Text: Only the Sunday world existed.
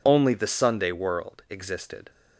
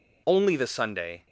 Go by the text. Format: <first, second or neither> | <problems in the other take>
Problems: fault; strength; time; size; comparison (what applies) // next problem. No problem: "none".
first | stops before "world existed"; at 1.2 s